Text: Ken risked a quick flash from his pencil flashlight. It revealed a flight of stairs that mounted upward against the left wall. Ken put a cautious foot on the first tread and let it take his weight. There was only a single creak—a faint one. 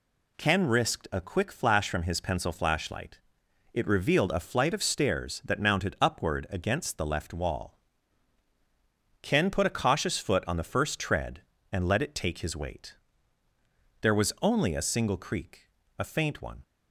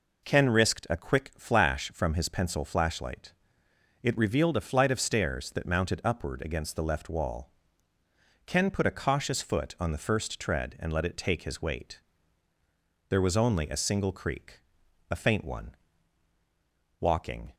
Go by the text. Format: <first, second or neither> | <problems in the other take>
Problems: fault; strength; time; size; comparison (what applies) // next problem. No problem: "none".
first | goes on to say "Walking"; from 17.0 s on; 0.54 s long